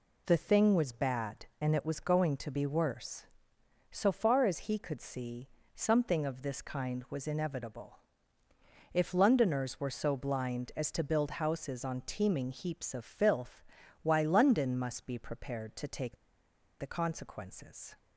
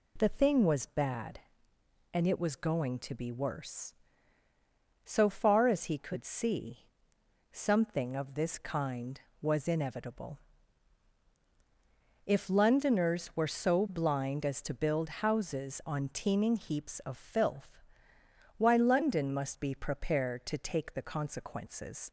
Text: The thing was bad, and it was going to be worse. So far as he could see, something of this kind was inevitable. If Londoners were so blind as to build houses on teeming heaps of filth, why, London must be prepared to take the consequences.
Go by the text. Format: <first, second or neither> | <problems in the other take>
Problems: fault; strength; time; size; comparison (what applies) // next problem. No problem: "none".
second | pauses between "take" and "the"; noticeable; at 16.1 s; 0.62 s long